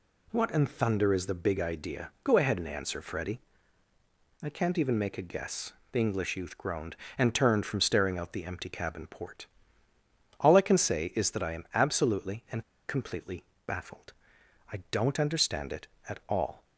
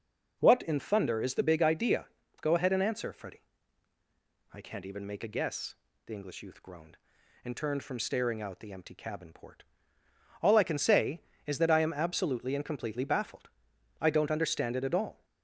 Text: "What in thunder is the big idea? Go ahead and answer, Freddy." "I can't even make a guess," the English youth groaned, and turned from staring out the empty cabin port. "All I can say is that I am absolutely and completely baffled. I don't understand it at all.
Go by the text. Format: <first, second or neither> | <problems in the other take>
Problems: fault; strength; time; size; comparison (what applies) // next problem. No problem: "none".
second | pauses between "and" and "completely"; slight; at 12.6 s; 0.25 s long // pauses between "completely" and "baffled"; slight; at 13.4 s; 0.22 s long